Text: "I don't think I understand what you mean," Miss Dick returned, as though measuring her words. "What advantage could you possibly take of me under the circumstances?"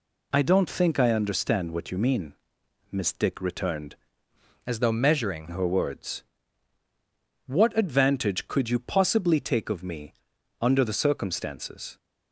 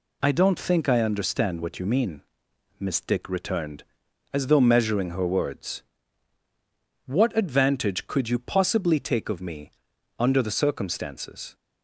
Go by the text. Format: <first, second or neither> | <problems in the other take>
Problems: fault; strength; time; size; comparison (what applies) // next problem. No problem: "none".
second | changes voice from "as" to "measuring"; from 4.6 to 5.4 s; 0.8 s long // pauses between "me" and "under"; noticeable; at 10.1 s; 0.48 s long; noticeable in the second